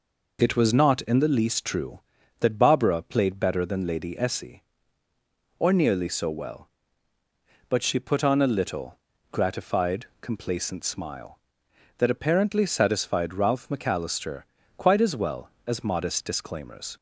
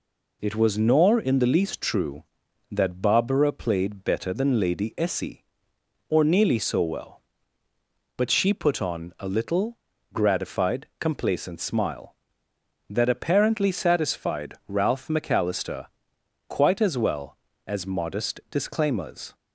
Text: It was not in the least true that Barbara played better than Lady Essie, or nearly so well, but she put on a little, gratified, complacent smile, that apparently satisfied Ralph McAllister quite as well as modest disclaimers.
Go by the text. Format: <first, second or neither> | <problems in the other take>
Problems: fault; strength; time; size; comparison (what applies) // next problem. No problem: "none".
first | says "nor" for "not"; at 0.7 s // pauses between "McAllister" and "quite"; noticeable; at 15.8 s; 0.62 s long; slight in the first